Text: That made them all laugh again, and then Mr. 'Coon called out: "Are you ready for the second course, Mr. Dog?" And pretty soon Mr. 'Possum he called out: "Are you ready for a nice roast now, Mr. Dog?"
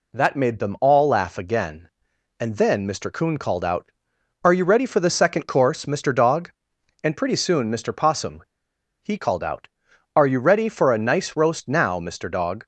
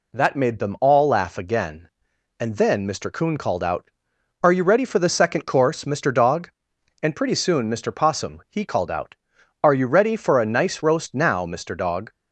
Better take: second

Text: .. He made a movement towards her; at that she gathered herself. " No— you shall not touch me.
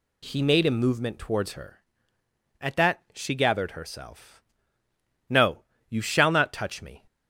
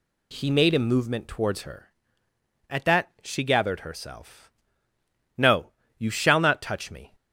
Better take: neither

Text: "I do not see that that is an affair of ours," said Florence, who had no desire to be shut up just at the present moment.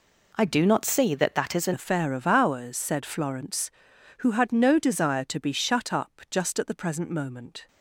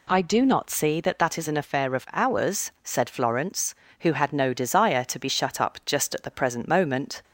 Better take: second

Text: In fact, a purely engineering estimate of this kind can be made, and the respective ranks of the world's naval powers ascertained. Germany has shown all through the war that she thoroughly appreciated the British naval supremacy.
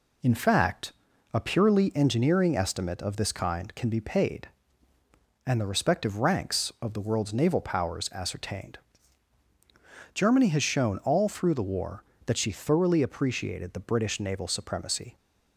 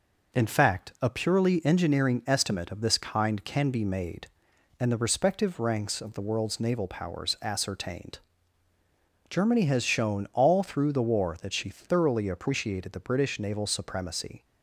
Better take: second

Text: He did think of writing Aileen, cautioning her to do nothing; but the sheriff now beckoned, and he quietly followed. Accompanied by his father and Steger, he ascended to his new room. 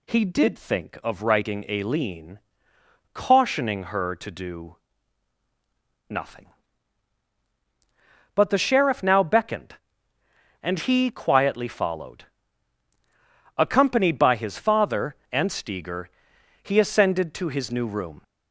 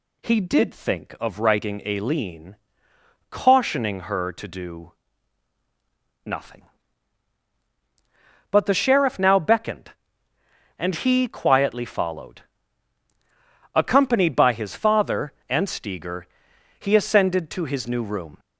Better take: neither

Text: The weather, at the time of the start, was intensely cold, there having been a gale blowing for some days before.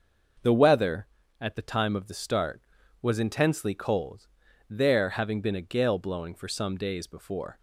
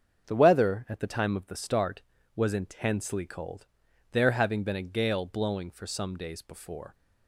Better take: neither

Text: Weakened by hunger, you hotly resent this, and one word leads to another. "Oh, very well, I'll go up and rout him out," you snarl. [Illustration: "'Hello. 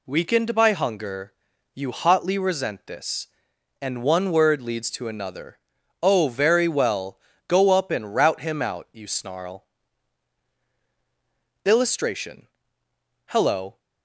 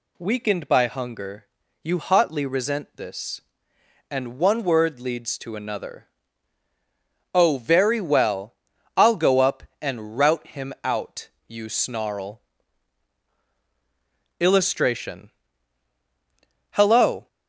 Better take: second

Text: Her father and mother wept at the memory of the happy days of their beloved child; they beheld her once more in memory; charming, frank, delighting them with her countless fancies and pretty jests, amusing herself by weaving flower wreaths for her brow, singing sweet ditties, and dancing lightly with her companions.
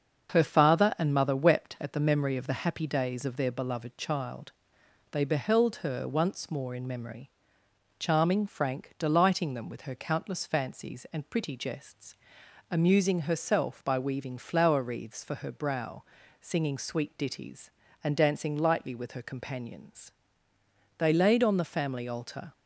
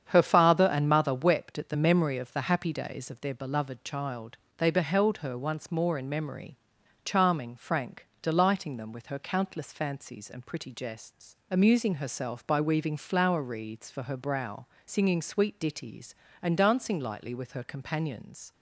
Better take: second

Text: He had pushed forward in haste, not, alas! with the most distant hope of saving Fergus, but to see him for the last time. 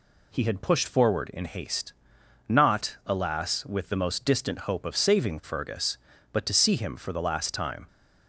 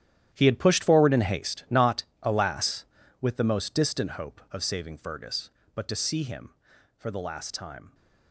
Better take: first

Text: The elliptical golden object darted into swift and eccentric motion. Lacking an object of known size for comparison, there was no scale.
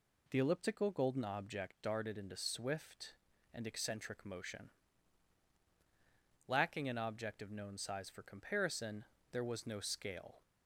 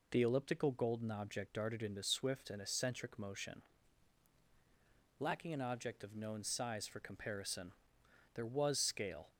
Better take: first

